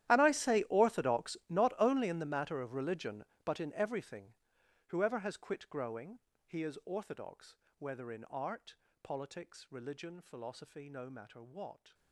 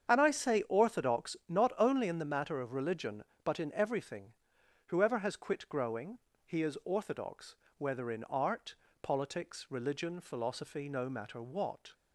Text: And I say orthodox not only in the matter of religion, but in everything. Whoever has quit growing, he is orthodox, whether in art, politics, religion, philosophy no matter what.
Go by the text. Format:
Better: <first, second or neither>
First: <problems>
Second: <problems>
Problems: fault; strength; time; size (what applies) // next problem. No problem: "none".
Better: second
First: gets quieter; strong; throughout; 20 dB // starts louder than the rest; strong; until 1.1 s; 12.5 dB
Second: starts louder than the rest; strong; until 1.1 s; 8 dB